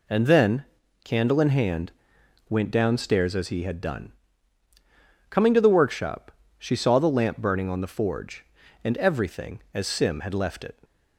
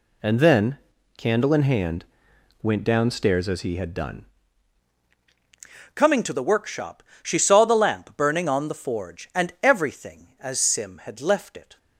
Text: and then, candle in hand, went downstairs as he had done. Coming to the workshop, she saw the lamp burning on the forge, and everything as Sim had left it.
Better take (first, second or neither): first